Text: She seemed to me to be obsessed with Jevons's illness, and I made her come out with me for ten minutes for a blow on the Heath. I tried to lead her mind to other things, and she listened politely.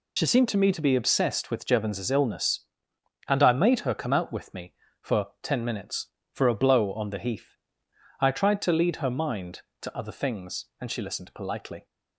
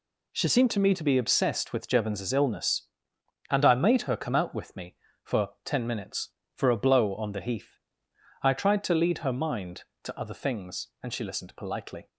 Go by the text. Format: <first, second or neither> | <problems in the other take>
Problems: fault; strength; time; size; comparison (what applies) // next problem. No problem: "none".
second | loses the start of "She"; at 0.1 s; 70 ms // pauses between "for" and "ten"; slight; at 5.2 s; 0.16 s long; slight in the second